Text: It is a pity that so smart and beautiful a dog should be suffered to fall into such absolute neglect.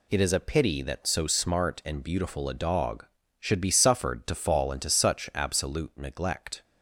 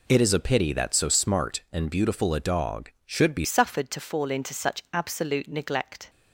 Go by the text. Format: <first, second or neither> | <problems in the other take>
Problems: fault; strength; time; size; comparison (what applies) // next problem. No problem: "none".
first | changes voice at "suffered"; from 3.4 s on; 2.6 s long